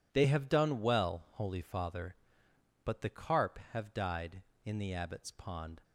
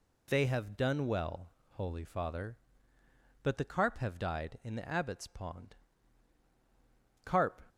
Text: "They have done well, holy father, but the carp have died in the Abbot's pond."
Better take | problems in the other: first | goes on to say "Carp"; slight; from 7.2 s on; 0.38 s long

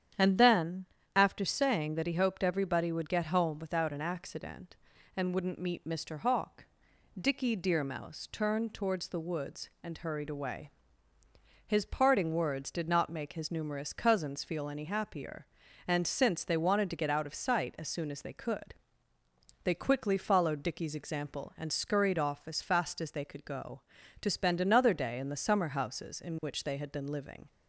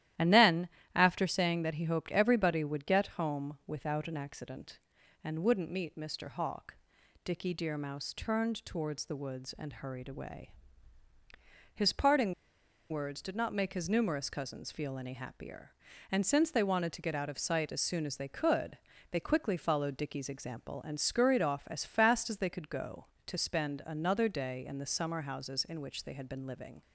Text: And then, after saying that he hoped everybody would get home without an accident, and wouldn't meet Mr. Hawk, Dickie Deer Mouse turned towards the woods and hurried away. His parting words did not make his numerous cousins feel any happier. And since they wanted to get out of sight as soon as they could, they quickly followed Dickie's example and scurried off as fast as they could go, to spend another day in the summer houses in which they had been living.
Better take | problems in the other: first | starts louder than the rest; strong; until 1.4 s; 13 dB; strong in the first // pauses between "parting" and "words"; noticeable; at 12.3 s; 0.56 s long

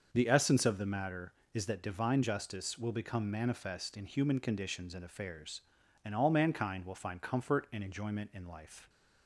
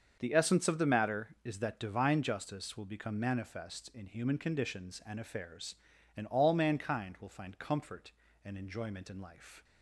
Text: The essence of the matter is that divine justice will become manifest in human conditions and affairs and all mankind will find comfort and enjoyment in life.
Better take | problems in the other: neither | starts louder than the rest; the same in both

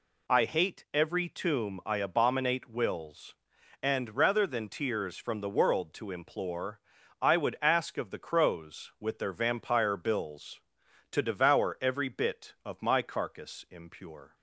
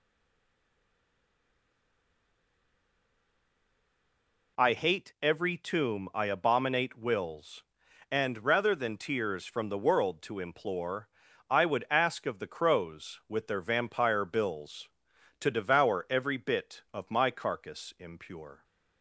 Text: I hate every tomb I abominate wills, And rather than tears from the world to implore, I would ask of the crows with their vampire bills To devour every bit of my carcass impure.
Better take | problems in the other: first | stays silent before the first word; strong; until 4.5 s; 4.5 s long

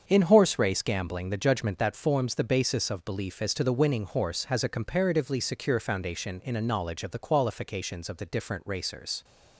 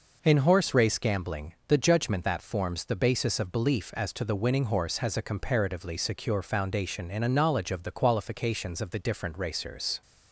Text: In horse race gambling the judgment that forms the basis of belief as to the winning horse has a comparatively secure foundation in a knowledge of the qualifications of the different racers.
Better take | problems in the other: second | gets quieter; strong; throughout; 8 dB

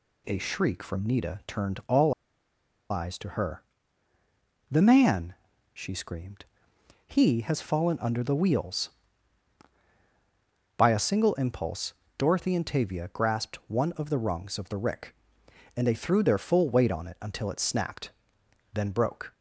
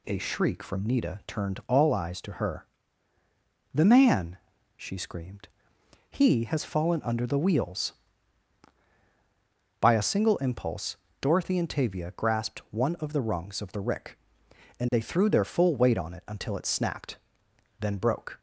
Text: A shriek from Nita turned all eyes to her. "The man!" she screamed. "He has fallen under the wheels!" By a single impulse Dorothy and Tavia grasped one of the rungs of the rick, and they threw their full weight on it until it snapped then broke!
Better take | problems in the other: second | pauses between "all" and "eyes"; noticeable; at 2.1 s; 0.78 s long // pauses between "impulse" and "Dorothy"; slight; at 11.9 s; 0.26 s long; slight in the second // pauses between "snapped" and "then"; noticeable; at 18.1 s; 0.64 s long; noticeable in the second

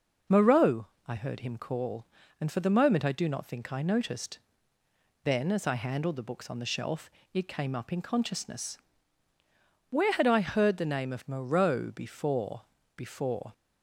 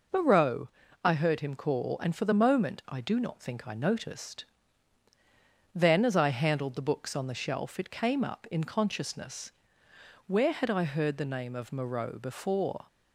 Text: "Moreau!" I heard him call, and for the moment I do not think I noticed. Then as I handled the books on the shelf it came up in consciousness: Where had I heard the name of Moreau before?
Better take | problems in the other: second | pauses between "shelf" and "it"; slight; at 7.0 s; 0.24 s long // says "before" twice; at 12.9 s

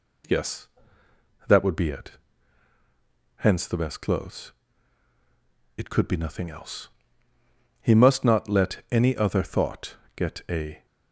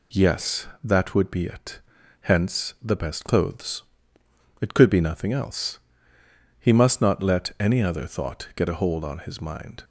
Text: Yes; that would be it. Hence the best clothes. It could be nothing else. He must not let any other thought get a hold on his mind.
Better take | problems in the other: second | pauses between "thought" and "get"; slight; at 9.9 s; 0.18 s long // stops before "hold on his mind"; at 10.8 s

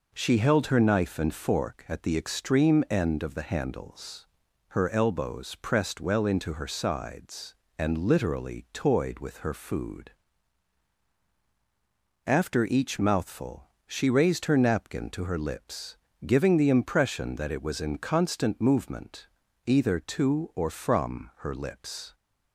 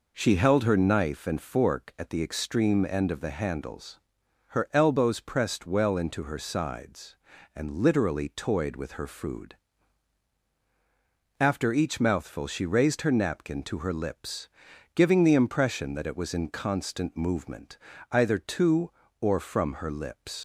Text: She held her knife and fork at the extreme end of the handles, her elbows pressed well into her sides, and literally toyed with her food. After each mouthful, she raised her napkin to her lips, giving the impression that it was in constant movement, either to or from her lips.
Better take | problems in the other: first | leaves "lips" unfinished; at 20.3 s; 110 ms

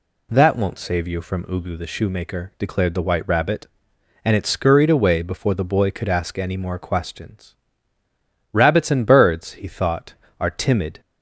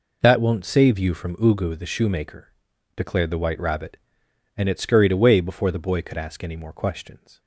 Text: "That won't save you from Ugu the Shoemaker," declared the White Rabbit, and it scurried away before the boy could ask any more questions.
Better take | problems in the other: second | goes on to say "Rabbits and birds he thought are timid"; strong; from 8.5 s on; 2.4 s long

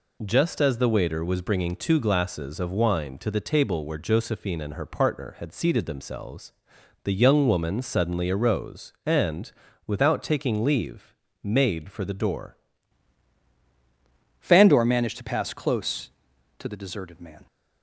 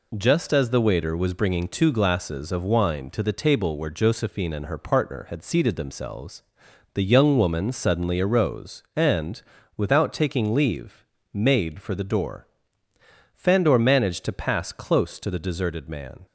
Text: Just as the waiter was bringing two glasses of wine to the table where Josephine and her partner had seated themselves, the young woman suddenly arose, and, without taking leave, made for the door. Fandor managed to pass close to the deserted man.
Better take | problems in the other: second | changes voice at "Fandor"; from 14.4 s on; 3.0 s long

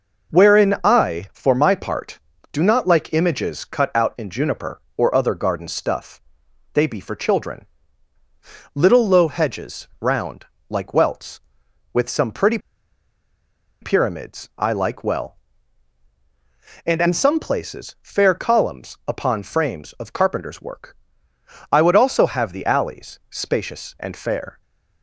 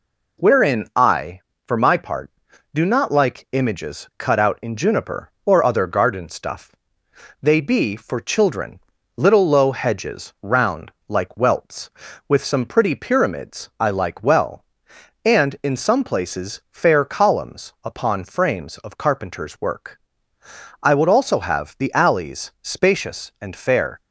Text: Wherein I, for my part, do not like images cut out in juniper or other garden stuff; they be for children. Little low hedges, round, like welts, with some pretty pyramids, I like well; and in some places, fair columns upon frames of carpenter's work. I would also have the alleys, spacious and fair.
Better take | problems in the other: second | pauses between "pretty" and "pyramids"; at 12.5 s; 1.2 s long

